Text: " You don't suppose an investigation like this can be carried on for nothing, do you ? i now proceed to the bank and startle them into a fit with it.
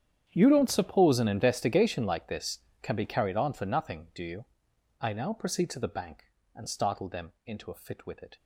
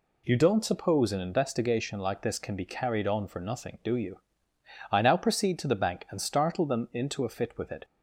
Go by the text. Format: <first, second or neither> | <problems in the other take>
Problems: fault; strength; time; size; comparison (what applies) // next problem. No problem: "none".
second | gets quieter; strong; throughout; 18 dB